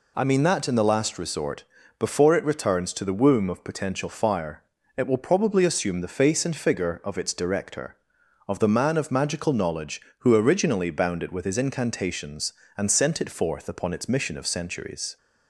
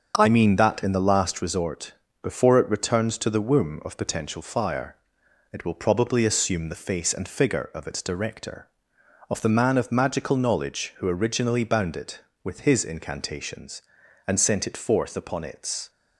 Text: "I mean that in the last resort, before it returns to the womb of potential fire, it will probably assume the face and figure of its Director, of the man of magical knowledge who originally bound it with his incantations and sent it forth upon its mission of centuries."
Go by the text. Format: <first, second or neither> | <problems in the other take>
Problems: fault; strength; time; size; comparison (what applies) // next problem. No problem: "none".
first | starts louder than the rest; until 1.1 s; 7 dB // stops before "mission of centuries"; at 15.8 s